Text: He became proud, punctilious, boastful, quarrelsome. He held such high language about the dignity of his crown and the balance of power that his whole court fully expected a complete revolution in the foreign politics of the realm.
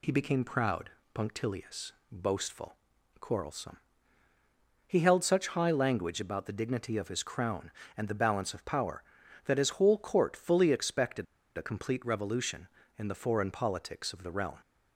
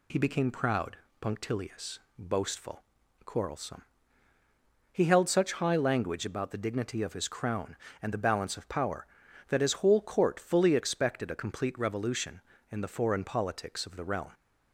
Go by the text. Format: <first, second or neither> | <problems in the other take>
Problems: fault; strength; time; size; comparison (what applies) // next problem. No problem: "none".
second | pauses between "expected" and "a"; slight; at 11.2 s; 0.31 s long